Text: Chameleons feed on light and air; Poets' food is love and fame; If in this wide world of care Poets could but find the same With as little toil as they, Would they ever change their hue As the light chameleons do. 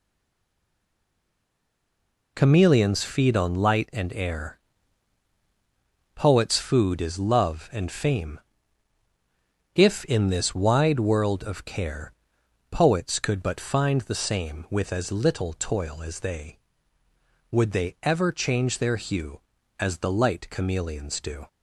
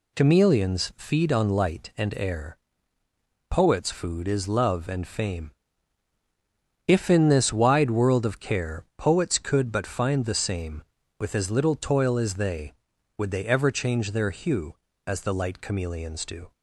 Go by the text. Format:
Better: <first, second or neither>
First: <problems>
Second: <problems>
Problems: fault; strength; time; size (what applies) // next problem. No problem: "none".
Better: second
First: stays silent before the first word; until 2.3 s; 2.3 s long // pauses between "care" and "Poets"; noticeable; at 12.1 s; 0.56 s long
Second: none